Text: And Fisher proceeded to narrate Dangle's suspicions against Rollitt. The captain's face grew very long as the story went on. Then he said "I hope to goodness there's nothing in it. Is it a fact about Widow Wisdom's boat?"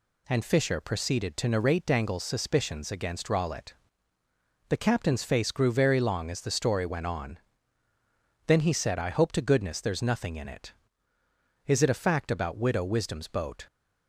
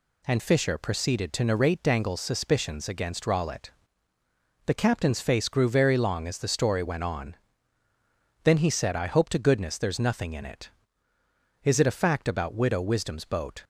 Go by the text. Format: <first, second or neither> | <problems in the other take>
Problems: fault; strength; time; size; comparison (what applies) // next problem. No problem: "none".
neither | none